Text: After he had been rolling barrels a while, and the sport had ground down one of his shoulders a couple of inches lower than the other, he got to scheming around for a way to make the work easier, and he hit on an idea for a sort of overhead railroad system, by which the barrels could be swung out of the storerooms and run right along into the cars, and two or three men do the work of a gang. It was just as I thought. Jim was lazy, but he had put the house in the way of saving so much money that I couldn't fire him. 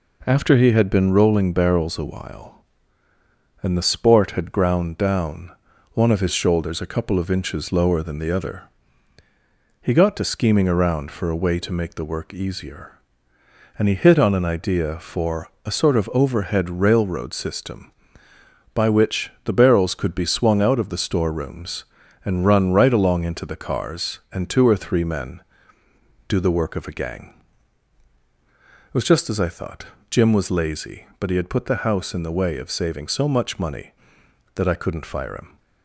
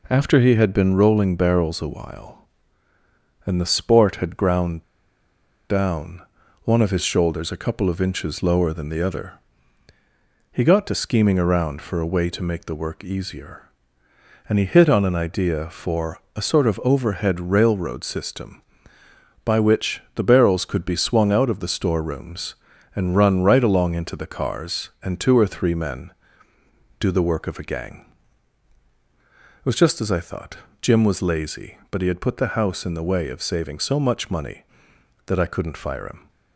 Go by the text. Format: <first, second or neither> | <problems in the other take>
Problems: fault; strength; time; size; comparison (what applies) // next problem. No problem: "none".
first | pauses between "ground" and "down"; noticeable; at 4.8 s; 0.87 s long // pauses between "down" and "one"; at 6.2 s; 0.42 s long; also in the first // pauses between "for" and "a"; slight; at 16.1 s; 0.16 s long; slight in the first // pauses between "which" and "the"; slight; at 20.0 s; 0.16 s long; slight in the first